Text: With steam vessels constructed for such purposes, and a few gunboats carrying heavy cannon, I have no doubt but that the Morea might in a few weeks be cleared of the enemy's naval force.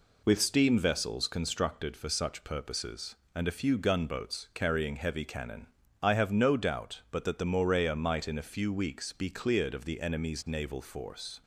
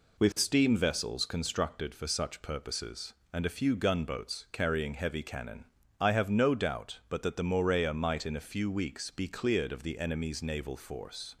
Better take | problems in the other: neither | none

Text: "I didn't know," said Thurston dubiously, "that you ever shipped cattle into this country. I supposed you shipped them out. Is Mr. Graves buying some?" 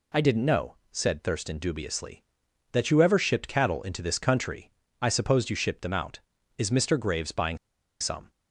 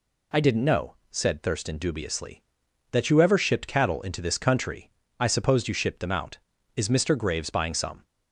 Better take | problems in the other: second | pauses between "buying" and "some"; at 7.5 s; 0.43 s long

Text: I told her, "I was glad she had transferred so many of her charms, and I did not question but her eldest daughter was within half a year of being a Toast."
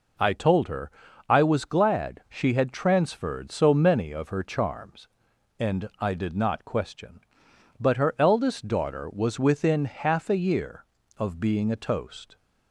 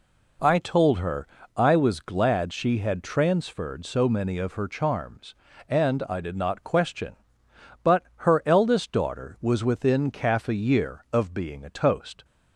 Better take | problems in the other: first | pauses between "but" and "her"; slight; at 8.0 s; 0.20 s long // says "calf" for "half"; at 10.1 s

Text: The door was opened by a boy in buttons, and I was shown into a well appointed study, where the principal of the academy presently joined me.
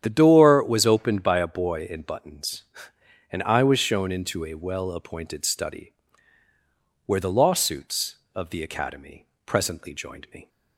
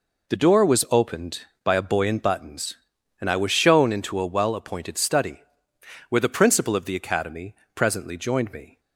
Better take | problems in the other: second | starts louder than the rest; strong; until 1.0 s; 9.5 dB // says "lawsuits" for "principal"; at 7.3 s // pauses between "academy" and "presently"; slight; at 9.2 s; 0.22 s long; slight in the second

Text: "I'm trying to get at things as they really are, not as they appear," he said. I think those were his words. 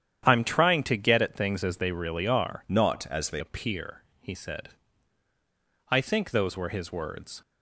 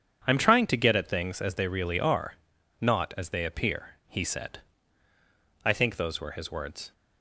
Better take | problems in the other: second | starts louder than the rest; strong; until 1.2 s; 9.5 dB; strong in the second // changes voice from "not" to "they"; from 2.6 to 3.4 s; 0.8 s long

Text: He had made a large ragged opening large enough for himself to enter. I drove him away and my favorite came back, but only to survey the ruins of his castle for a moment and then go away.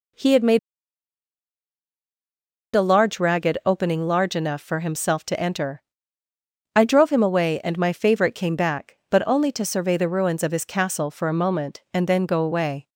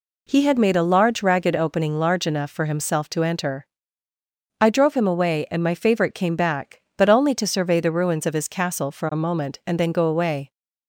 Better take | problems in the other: second | pauses between "made" and "a"; strong; at 0.5 s; 2.1 s long

